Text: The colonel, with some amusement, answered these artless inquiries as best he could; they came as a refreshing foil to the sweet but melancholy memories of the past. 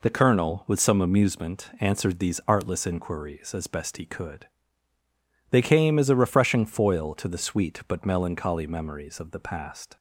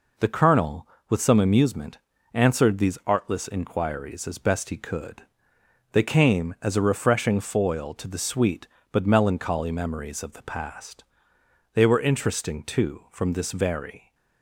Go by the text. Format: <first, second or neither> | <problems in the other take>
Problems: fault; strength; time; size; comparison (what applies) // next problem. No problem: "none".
first | goes on to say "They were interesting too from this very"; strong; from 11.7 s on; 2.4 s long